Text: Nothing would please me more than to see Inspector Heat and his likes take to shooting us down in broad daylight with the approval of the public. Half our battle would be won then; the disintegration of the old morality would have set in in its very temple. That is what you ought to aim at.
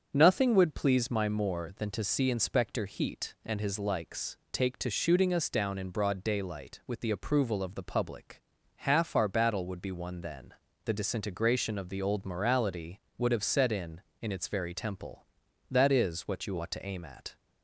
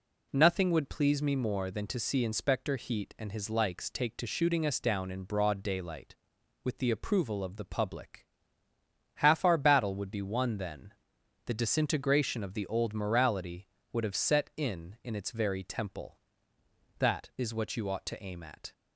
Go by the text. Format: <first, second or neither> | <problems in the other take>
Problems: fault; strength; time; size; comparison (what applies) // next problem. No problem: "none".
second | starts louder than the rest; strong; until 1.1 s; 7.5 dB // says "my" for "me"; at 1.1 s